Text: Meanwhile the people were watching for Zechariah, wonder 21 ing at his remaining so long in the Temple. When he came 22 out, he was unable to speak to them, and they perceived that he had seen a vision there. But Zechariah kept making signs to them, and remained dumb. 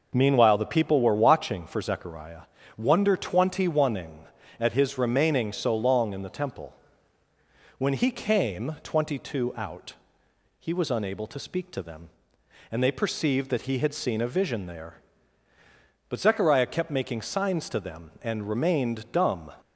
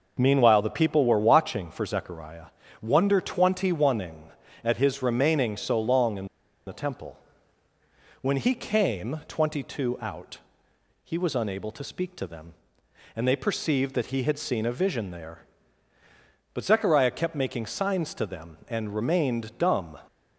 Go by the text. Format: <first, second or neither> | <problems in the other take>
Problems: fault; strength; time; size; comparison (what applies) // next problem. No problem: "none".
first | pauses between "in" and "the"; at 6.2 s; 0.40 s long